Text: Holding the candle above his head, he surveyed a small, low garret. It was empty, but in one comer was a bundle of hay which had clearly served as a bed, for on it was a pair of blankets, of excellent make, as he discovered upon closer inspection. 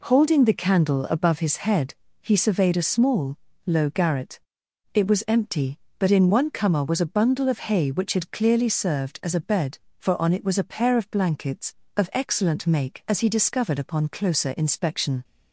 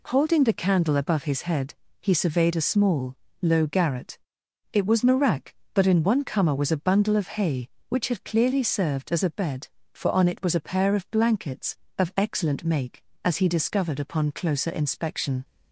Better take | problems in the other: first | says "marak" for "empty"; at 5.0 s

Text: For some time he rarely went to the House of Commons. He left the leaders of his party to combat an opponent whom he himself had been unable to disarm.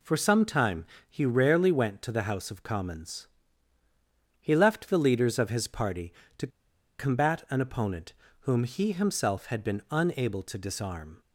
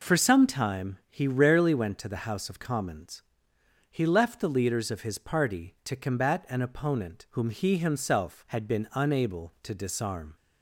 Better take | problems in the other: second | pauses between "time" and "he"; slight; at 0.8 s; 0.24 s long // pauses between "to" and "combat"; noticeable; at 6.4 s; 0.51 s long // pauses between "opponent" and "whom"; slight; at 8.1 s; 0.28 s long

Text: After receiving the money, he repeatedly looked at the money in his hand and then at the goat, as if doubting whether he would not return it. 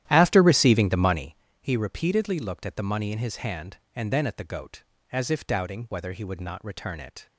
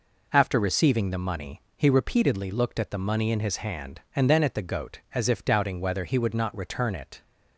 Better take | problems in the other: second | starts louder than the rest; strong; until 1.4 s; 12 dB

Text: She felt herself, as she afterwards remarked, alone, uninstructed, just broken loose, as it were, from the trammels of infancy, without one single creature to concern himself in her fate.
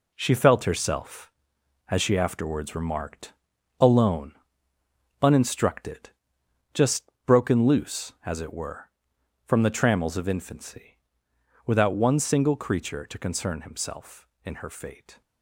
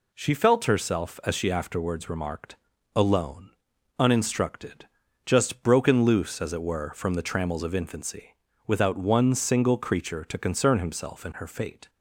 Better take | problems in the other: second | gets quieter; strong; throughout; 8 dB // pauses between "just" and "broken"; slight; at 7.0 s; 0.20 s long

